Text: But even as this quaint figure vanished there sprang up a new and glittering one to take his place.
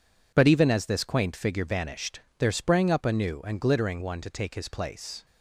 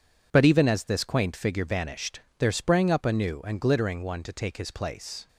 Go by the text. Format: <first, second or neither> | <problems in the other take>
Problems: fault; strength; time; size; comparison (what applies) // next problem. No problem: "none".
neither | pauses between "vanished" and "there"; slight; the same in both